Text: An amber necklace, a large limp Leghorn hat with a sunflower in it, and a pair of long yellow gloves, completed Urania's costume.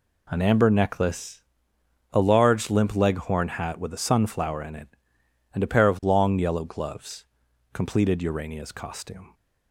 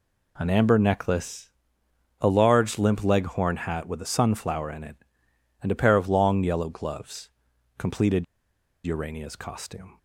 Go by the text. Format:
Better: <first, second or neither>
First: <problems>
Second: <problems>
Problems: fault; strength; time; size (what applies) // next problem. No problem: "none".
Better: first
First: none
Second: pauses between "completed" and "Urania's"; noticeable; at 8.2 s; 0.60 s long